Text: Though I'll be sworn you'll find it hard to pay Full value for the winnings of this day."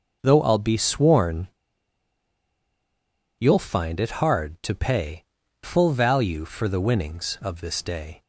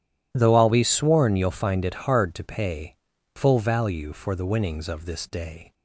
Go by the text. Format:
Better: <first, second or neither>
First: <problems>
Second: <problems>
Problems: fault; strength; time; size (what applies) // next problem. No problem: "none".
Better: second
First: pauses between "sworn" and "you'll"; strong; at 1.4 s; 1.9 s long // pauses between "pay" and "Full"; at 5.2 s; 0.38 s long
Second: pauses between "pay" and "Full"; at 2.9 s; 0.40 s long